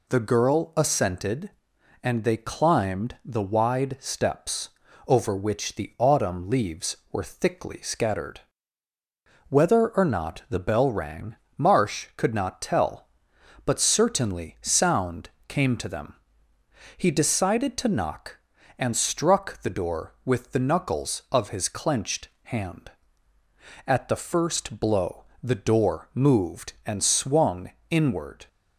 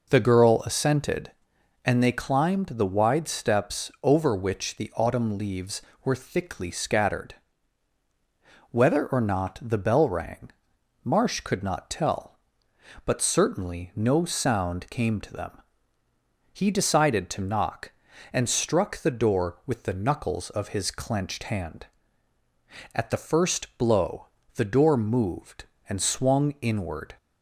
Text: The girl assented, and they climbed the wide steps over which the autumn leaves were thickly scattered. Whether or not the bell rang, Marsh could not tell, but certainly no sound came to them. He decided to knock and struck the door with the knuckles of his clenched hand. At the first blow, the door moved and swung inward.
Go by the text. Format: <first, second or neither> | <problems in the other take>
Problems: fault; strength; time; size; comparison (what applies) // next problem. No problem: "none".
second | pauses between "steps" and "over"; at 4.6 s; 0.38 s long // skips "no"; at 14.5 s // pauses between "sound" and "came"; slight; at 15.2 s; 0.18 s long // pauses between "clenched" and "hand"; slight; at 22.2 s; 0.16 s long // pauses between "swung" and "inward"; slight; at 27.7 s; 0.18 s long